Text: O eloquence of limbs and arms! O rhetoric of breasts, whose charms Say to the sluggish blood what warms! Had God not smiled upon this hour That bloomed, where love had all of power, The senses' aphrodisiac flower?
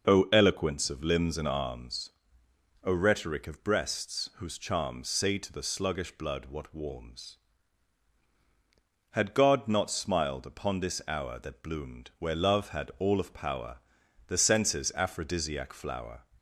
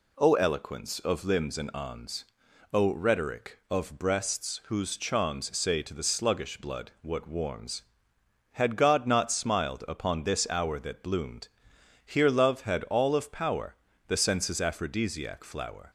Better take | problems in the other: first | says "here" for "where"; at 12.0 s

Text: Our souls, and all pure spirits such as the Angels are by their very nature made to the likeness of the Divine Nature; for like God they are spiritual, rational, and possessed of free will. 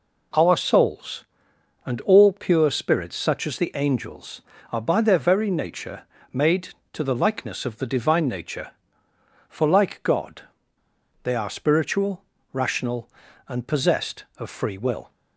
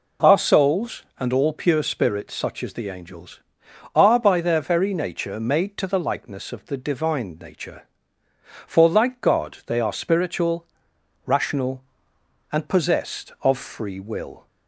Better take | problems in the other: second | pauses between "nature" and "made"; slight; at 6.0 s; 0.28 s long // pauses between "God" and "they"; noticeable; at 10.4 s; 0.79 s long

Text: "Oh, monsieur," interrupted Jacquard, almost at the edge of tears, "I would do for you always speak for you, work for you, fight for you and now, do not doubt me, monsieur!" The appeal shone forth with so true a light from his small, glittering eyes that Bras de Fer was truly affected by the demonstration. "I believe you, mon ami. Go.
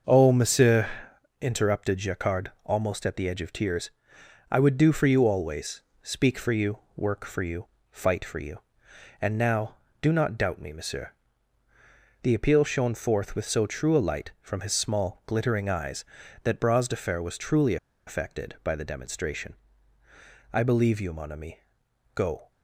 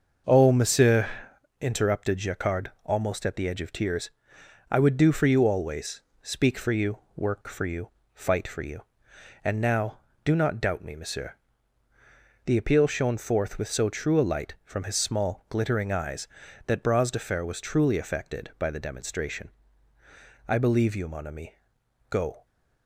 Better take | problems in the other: second | starts louder than the rest; noticeable; until 1.5 s; 6 dB; noticeable in the second // pauses between "always" and "speak"; slight; at 5.8 s; 0.22 s long; slight in the second // pauses between "truly" and "affected"; slight; at 17.7 s; 0.30 s long

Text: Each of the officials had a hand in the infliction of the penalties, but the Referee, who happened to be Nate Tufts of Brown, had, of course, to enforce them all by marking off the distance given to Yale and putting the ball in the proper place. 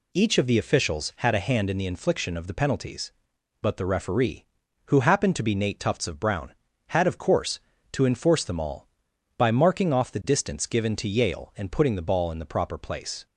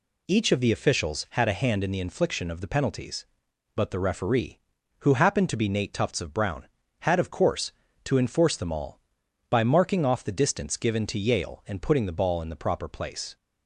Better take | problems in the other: neither | none

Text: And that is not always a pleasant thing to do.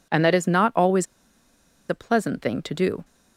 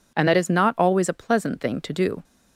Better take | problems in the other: second | pauses between "always" and "a"; noticeable; at 1.0 s; 0.84 s long

